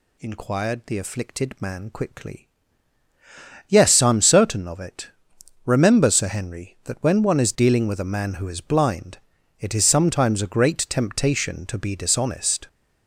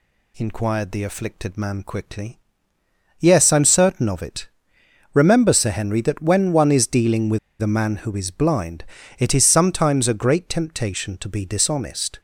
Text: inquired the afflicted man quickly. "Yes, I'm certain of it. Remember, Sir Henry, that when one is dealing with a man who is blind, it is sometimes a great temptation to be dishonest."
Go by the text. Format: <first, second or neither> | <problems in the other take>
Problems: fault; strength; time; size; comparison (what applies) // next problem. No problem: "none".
first | pauses between "with" and "a"; slight; at 7.3 s; 0.23 s long